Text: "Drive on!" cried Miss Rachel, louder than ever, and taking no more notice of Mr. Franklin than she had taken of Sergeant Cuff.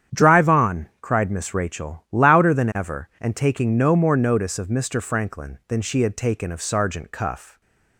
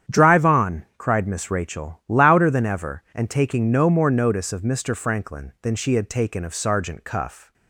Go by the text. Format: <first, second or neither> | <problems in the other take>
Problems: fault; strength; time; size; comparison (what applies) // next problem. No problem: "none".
neither | starts louder than the rest; strong; the same in both